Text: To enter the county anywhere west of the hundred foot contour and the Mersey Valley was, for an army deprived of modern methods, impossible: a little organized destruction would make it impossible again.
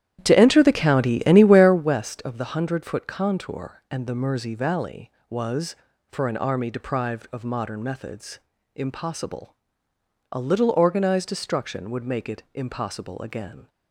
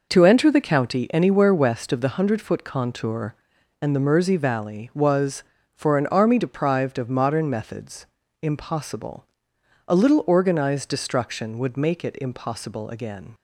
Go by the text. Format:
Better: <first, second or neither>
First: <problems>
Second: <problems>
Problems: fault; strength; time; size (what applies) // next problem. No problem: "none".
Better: second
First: starts louder than the rest; strong; until 1.9 s; 11 dB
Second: none